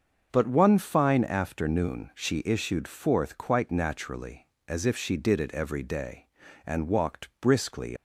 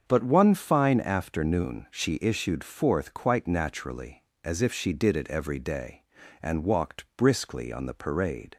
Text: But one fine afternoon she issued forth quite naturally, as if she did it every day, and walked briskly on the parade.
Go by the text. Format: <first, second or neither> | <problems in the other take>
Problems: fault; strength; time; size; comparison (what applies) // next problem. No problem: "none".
second | starts louder than the rest; until 1.3 s; 6.5 dB; also in the second // stops before "on the parade"; at 7.9 s